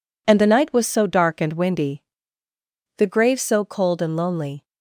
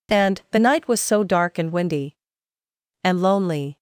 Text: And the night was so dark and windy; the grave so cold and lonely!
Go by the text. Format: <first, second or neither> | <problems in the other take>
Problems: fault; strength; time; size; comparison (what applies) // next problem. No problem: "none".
first | skips "the grave so cold"; at 2.5 s